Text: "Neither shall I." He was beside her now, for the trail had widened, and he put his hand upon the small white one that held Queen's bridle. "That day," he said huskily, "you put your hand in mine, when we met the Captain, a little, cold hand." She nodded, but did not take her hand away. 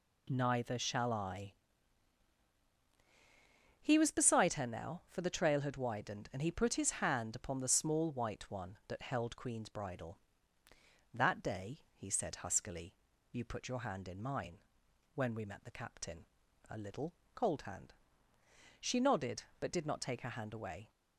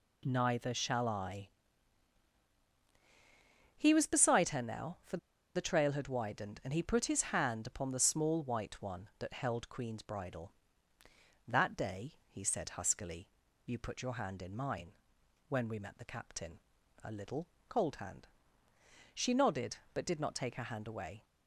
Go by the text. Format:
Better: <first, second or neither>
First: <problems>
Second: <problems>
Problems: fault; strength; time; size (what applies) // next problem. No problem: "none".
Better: first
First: none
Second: pauses between "for" and "the"; at 5.1 s; 0.37 s long